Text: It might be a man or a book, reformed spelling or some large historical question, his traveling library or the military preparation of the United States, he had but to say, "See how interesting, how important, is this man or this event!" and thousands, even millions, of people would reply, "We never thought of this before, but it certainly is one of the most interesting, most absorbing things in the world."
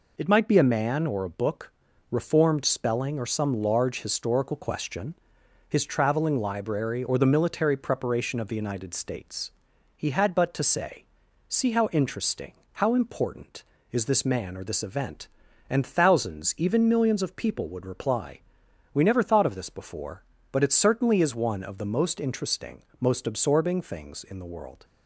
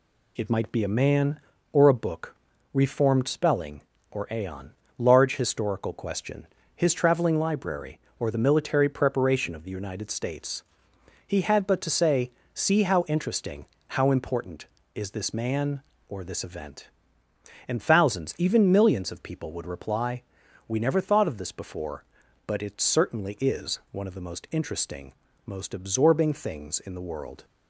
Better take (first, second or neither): first